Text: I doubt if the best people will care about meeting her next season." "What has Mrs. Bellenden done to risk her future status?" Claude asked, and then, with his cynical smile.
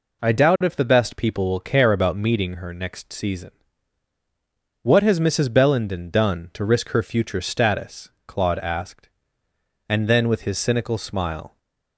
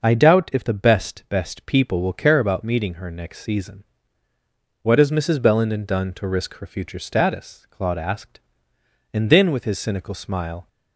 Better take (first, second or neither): first